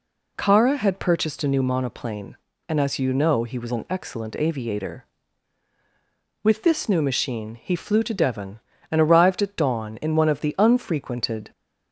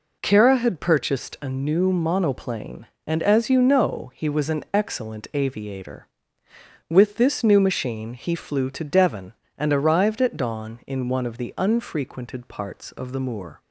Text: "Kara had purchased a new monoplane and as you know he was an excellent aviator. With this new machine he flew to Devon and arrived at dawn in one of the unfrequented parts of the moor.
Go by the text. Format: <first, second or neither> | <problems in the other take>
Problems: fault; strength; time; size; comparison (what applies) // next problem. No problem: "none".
second | stops before "parts of the moor"; at 11.5 s